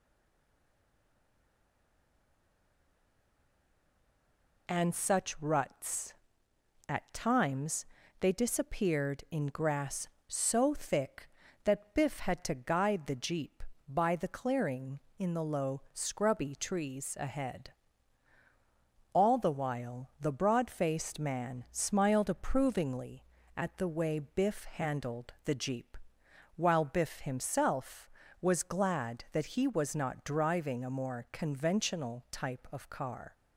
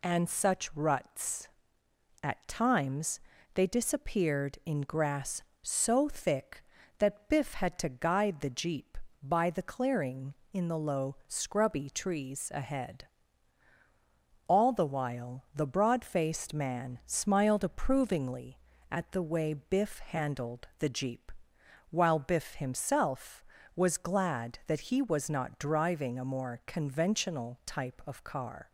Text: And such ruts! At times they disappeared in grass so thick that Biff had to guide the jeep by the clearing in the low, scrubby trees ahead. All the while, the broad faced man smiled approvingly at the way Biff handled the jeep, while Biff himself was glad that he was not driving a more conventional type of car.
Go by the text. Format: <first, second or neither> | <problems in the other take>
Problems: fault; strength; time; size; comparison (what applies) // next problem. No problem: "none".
second | stays silent before the first word; strong; until 4.6 s; 4.6 s long // pauses between "times" and "they"; slight; at 7.8 s; 0.36 s long; slight in the second